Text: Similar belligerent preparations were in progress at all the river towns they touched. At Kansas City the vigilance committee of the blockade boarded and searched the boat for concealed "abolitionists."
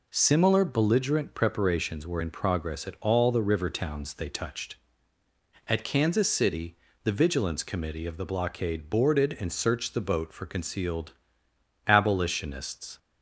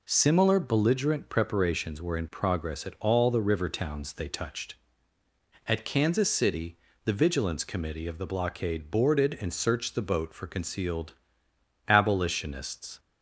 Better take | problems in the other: neither | pauses between "City" and "the"; slight; the same in both // pauses between "concealed" and "abolitionists"; noticeable; the same in both

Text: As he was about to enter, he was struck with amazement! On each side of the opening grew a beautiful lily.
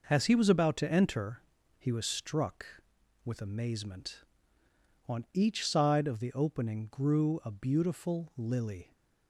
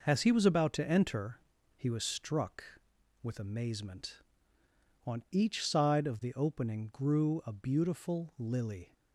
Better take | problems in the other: neither | none

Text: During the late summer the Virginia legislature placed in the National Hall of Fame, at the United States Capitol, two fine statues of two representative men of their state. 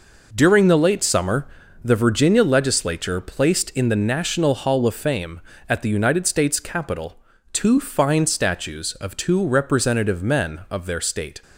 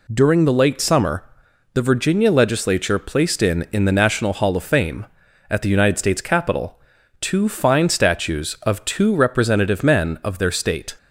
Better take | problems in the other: first | pauses between "summer" and "the"; noticeable; at 1.2 s; 0.50 s long; slight in the first // says "in" twice; at 3.7 s

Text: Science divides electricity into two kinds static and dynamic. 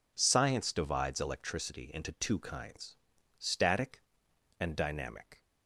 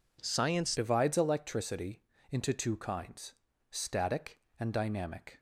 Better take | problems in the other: first | changes voice at "divides"; from 0.7 s on; 4.6 s long // pauses between "electricity" and "into"; slight; at 2.0 s; 0.28 s long // pauses between "kinds" and "static"; at 3.3 s; 0.38 s long; also in the first

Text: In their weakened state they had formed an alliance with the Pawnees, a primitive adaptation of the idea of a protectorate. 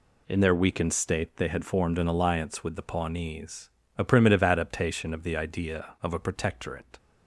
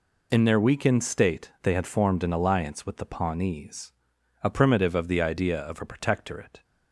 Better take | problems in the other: first | skips "adaptation"; at 4.9 s

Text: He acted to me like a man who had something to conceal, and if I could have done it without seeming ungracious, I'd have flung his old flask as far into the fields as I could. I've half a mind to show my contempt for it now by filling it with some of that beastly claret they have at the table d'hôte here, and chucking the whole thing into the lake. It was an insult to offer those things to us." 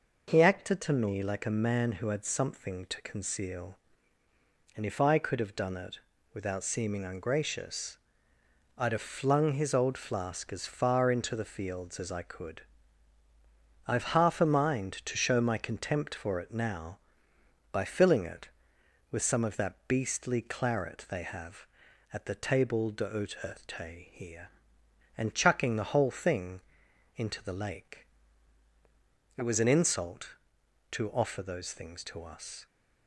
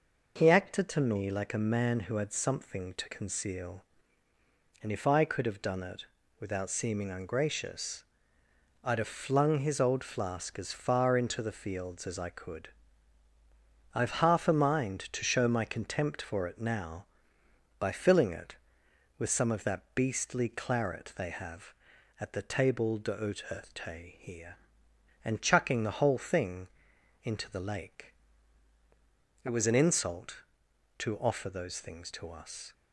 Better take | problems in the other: neither | pauses between "it" and "without"; slight; the same in both // pauses between "thing" and "into"; noticeable; the same in both

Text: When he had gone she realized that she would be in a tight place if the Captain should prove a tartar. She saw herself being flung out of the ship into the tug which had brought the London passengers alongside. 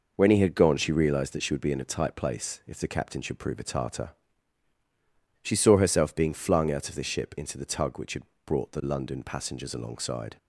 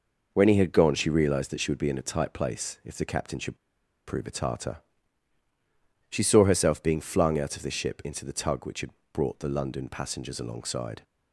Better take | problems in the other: first | pauses between "should" and "prove"; noticeable; at 3.5 s; 0.49 s long // pauses between "had" and "brought"; slight; at 8.8 s; 0.24 s long; slight in the first

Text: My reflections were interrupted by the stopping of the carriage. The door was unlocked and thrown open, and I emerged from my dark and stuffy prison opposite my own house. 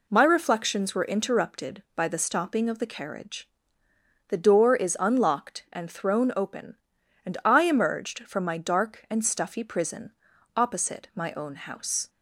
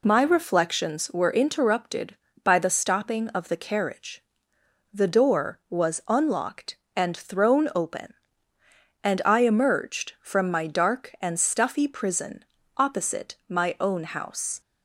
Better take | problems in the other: second | says "is" for "was"; at 4.7 s // pauses between "prison" and "opposite"; at 10.1 s; 0.44 s long; slight in the second

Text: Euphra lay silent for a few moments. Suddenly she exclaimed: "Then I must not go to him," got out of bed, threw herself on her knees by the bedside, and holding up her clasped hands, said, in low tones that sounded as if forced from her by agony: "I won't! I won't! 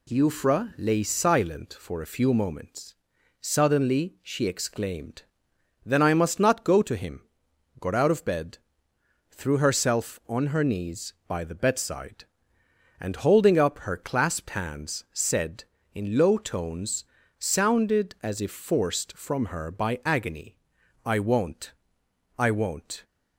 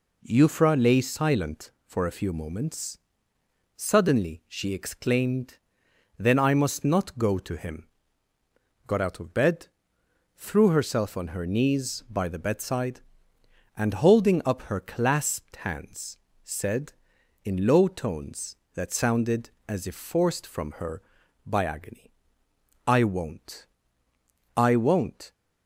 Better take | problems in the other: second | skips "that"; at 17.2 s

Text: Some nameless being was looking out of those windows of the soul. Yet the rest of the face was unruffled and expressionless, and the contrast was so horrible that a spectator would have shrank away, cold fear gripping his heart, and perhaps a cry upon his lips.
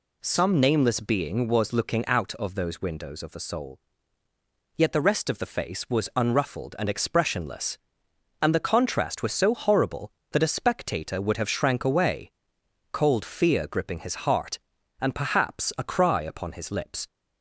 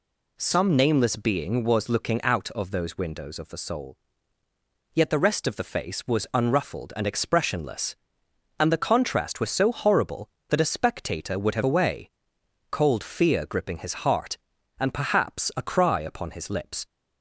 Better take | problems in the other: first | skips "shrank"; at 11.6 s

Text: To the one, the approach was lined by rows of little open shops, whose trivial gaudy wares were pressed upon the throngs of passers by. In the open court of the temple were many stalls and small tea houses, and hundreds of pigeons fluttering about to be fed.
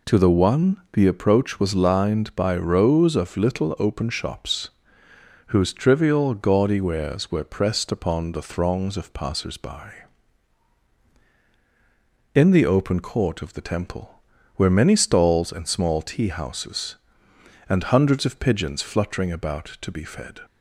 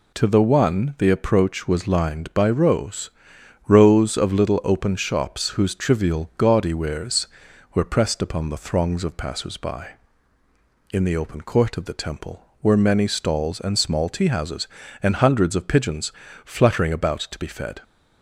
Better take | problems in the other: first | says "rows" twice; at 3.6 s // pauses between "pigeons" and "fluttering"; slight; at 16.1 s; 0.34 s long

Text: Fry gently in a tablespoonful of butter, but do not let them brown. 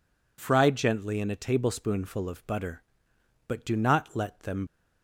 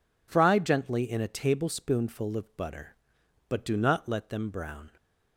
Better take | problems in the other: second | stops before "brown"; at 4.6 s

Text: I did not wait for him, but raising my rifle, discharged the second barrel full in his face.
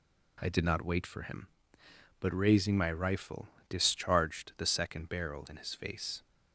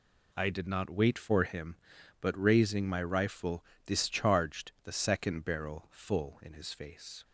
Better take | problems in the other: second | skips "full"; at 5.4 s

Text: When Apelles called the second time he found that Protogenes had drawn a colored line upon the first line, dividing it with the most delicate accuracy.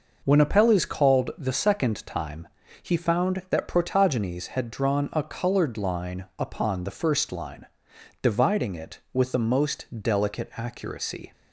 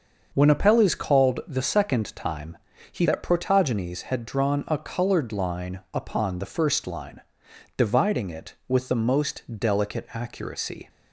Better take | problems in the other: first | starts louder than the rest; until 1.3 s; 6 dB // pauses between "time" and "he"; slight; at 2.5 s; 0.34 s long; slight in the first // skips "found"; at 3.0 s // pauses between "most" and "delicate"; slight; at 9.4 s; 0.16 s long; slight in the first

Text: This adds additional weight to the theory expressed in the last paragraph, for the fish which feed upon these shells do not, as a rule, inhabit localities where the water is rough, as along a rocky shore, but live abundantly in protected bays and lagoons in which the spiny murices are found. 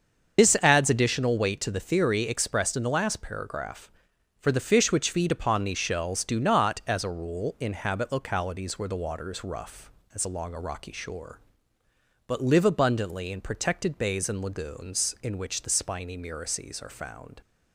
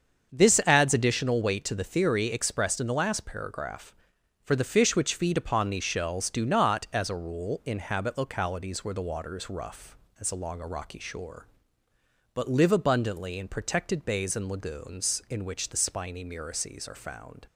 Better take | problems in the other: second | loses the start of "This"; at 0.3 s; 110 ms // starts louder than the rest; until 1.4 s; 7 dB; also in the second

